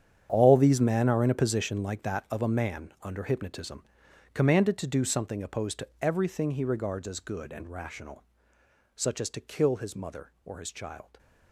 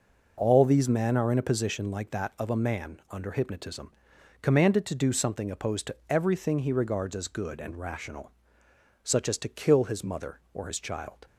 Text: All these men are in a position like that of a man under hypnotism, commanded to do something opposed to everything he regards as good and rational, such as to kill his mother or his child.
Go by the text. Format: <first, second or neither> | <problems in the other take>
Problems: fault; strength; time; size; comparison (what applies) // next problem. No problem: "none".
second | gets quieter; strong; throughout; 15 dB